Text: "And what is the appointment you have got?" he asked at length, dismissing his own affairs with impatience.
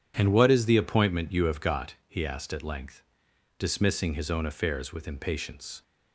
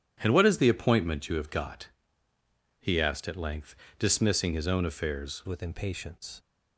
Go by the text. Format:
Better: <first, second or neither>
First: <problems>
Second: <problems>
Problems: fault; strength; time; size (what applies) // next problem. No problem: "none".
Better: first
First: none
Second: starts louder than the rest; strong; until 1.2 s; 10 dB // changes voice at "with"; from 5.4 s on; 0.9 s long